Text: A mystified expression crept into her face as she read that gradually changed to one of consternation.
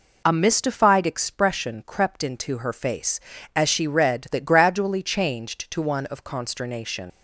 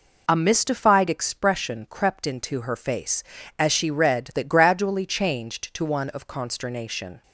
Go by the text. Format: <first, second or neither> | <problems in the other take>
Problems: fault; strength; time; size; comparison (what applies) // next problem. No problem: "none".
second | leaves "consternation" unfinished; at 7.1 s; 90 ms